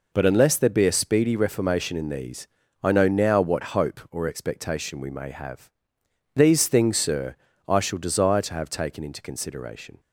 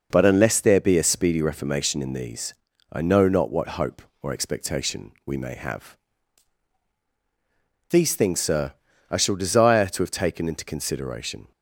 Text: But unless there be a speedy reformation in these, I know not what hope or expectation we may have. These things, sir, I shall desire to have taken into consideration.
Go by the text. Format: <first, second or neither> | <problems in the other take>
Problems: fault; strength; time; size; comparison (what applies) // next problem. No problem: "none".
second | says "now" for "not"; at 3.0 s